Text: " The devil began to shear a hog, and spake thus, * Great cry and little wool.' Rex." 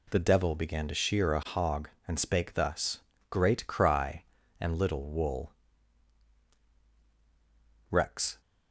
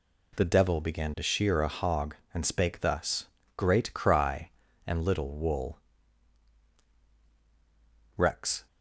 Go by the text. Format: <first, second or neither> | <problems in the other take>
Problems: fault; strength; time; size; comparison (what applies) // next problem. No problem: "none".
neither | none